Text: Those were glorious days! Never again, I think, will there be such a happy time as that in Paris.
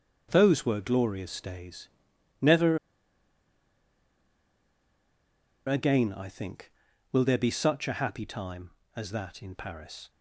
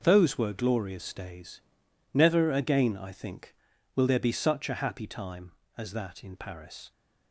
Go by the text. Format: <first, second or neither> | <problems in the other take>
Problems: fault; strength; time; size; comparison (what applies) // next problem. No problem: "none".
second | pauses between "Never" and "again"; strong; at 2.7 s; 2.8 s long